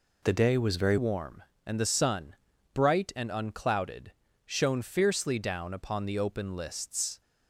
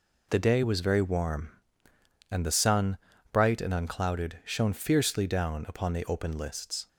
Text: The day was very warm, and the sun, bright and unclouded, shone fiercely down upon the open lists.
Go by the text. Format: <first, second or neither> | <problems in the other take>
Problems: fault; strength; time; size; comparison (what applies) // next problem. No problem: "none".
second | changes voice at "warm"; from 0.9 s on; 6.3 s long